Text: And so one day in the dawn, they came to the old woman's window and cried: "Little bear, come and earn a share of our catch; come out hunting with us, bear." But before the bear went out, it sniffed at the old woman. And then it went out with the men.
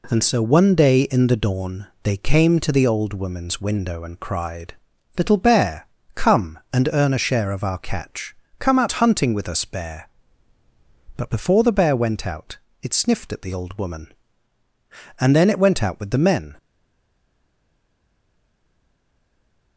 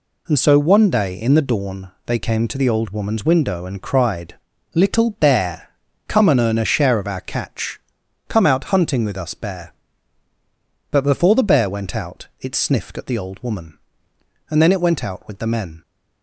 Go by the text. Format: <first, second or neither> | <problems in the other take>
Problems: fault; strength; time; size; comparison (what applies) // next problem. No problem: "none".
second | stays silent after the last word; strong; from 16.5 s on; 3.2 s long